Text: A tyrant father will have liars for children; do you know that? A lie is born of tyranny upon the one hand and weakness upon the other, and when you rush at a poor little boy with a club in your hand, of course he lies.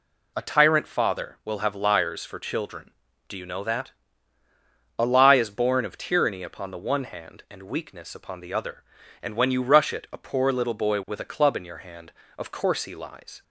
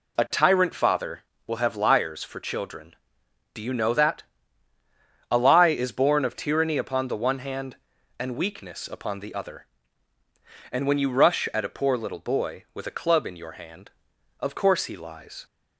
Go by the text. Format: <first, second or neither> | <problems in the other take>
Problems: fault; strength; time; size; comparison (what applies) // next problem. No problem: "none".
second | says "it" for "at"; at 9.9 s